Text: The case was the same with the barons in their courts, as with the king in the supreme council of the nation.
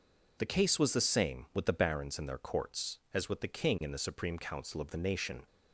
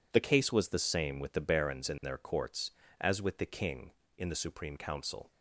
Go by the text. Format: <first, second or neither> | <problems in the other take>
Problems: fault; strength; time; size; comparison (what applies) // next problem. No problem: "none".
first | stops before "of the nation"; at 5.3 s